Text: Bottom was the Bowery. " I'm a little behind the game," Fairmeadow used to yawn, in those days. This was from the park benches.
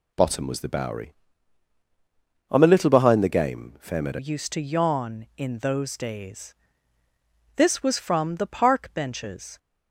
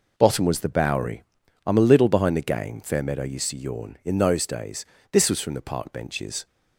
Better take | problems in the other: second | changes voice at "used"; from 4.1 s on; 5.4 s long

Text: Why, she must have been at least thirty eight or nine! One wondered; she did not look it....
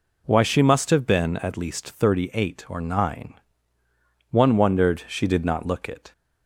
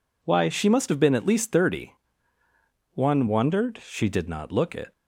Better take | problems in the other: first | skips "eight or nine"; at 2.4 s

